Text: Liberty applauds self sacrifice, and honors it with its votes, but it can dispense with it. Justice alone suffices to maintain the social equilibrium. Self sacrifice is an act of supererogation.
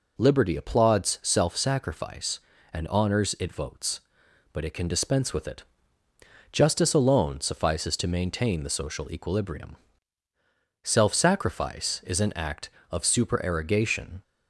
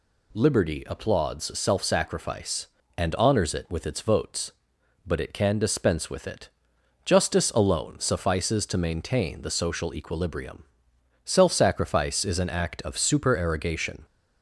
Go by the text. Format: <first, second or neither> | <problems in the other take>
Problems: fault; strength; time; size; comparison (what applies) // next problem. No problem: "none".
second | skips "with its"; at 3.5 s